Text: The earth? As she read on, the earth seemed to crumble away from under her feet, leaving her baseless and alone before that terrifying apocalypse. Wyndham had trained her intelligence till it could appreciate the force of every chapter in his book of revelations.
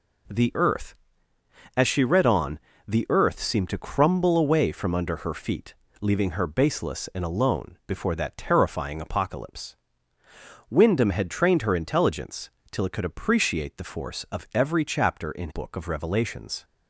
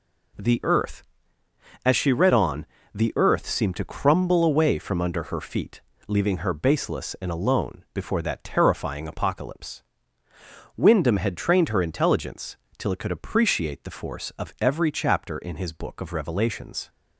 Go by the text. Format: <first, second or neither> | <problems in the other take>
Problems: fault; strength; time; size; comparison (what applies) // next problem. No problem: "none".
second | pauses between "intelligence" and "till"; slight; at 12.5 s; 0.22 s long; slight in the second // skips "his"; at 15.4 s